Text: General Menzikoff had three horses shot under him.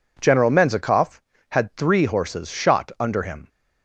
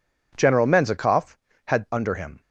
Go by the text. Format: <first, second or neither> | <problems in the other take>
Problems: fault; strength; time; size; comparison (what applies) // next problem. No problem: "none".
first | skips "three horses shot"; at 1.9 s